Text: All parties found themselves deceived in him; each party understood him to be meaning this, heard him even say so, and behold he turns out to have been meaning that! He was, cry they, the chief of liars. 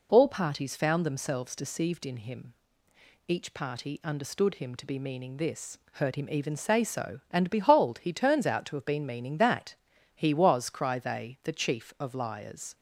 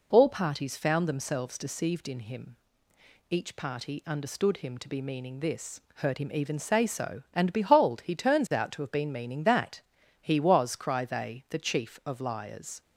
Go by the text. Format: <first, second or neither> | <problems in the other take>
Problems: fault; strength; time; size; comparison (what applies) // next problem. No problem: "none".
neither | none